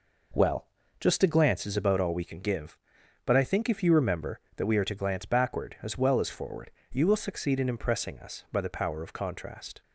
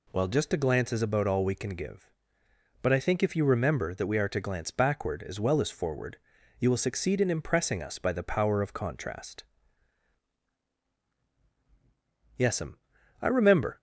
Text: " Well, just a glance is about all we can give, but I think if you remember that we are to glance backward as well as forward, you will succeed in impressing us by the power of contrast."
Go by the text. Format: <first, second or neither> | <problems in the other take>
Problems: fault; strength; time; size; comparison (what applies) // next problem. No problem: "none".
first | goes on to say "Yes'm I remember"; from 12.3 s on; 1.4 s long